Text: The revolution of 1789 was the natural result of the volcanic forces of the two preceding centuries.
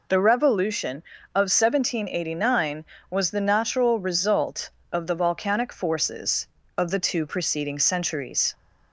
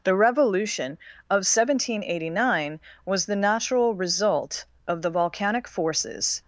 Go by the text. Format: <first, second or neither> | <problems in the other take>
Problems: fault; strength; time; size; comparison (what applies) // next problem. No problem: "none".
first | stops before "of the two preceding centuries"; at 6.4 s